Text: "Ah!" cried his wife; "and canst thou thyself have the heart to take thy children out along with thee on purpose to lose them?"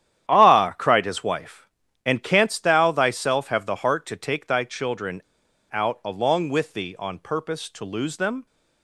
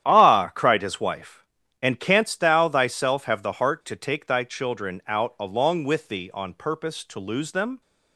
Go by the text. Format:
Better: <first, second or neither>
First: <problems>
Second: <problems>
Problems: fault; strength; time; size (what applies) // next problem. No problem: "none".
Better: second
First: starts louder than the rest; strong; until 1.3 s; 10.5 dB // pauses between "children" and "out"; noticeable; at 5.2 s; 0.46 s long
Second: starts louder than the rest; strong; until 1.0 s; 10.5 dB